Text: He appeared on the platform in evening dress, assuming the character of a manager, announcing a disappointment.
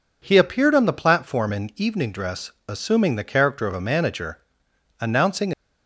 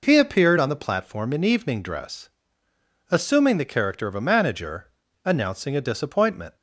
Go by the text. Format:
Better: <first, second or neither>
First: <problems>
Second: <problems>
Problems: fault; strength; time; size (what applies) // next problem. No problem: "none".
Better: second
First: stops before "a disappointment"; at 5.5 s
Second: none